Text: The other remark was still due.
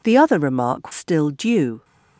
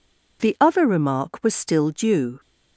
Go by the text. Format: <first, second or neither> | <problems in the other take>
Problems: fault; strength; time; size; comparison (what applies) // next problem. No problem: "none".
second | skips "was"; at 0.9 s